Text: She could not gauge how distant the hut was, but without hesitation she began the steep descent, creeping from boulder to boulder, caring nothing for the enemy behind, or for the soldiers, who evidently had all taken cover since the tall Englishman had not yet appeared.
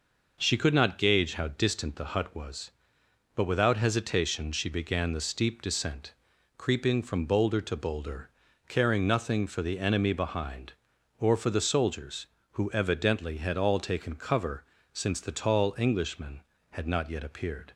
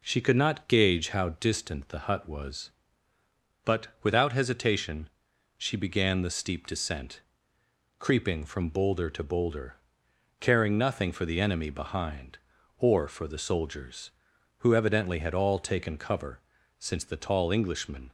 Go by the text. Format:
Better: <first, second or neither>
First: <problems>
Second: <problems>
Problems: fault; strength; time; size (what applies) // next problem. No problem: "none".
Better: first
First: pauses between "cover" and "since"; slight; at 14.6 s; 0.30 s long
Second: pauses between "but" and "without"; slight; at 3.8 s; 0.16 s long // pauses between "hesitation" and "she"; noticeable; at 5.0 s; 0.48 s long // pauses between "cover" and "since"; at 16.4 s; 0.40 s long // stops before "had not yet appeared"; at 18.0 s